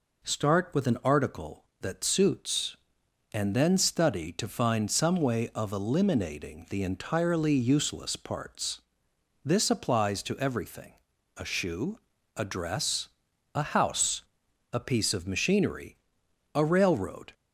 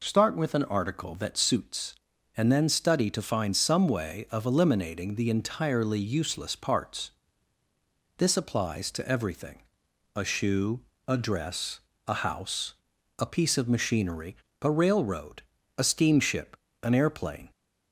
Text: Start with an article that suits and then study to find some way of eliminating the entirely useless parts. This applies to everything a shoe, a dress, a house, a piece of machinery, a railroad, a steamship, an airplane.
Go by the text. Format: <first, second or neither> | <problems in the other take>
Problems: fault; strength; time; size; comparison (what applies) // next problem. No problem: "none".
second | pauses between "everything" and "a"; at 10.9 s; 0.42 s long; noticeable in the second // stops before "a steamship an airplane"; at 17.3 s